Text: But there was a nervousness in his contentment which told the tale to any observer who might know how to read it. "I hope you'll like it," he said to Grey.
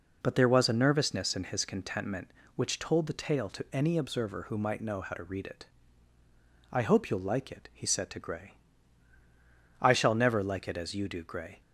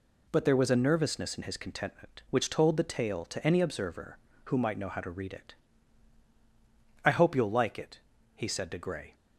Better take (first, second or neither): second